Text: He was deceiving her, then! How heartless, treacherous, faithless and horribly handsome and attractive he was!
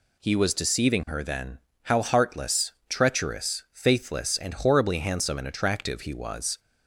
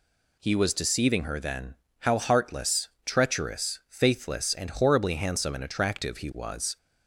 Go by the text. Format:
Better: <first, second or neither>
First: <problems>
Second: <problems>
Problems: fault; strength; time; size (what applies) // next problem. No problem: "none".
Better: neither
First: none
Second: none